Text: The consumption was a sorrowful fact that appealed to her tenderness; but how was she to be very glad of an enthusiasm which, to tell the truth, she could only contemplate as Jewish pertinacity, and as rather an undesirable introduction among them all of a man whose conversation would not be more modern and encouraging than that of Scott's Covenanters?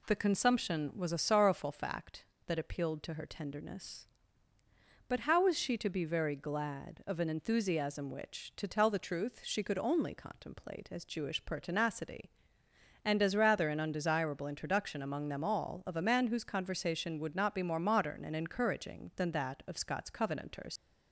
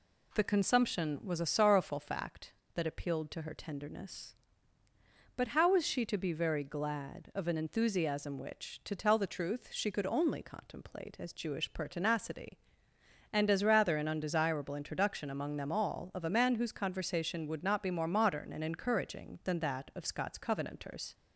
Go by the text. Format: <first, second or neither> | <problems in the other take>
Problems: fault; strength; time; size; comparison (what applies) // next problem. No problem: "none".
second | leaves "Covenanters" unfinished; at 20.7 s; 100 ms